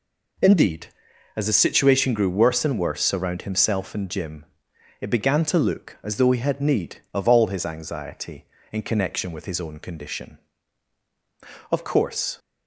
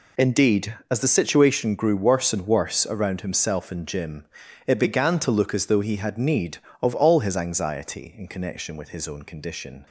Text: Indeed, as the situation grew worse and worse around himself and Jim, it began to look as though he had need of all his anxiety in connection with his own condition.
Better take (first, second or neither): second